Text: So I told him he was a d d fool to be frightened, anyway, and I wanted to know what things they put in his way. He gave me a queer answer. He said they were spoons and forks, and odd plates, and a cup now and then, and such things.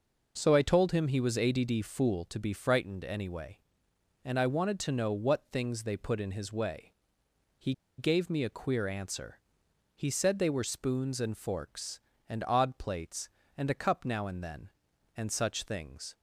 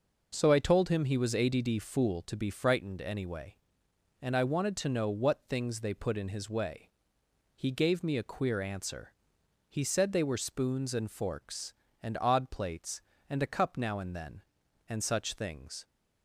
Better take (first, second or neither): second